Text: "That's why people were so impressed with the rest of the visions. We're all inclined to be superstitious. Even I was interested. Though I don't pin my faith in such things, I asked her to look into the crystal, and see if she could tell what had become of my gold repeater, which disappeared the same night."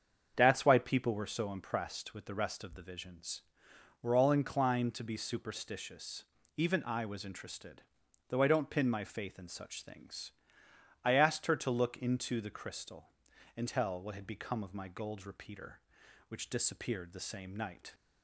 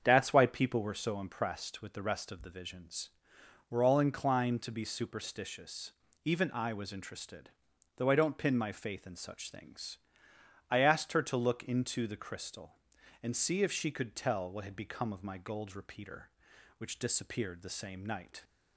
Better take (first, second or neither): second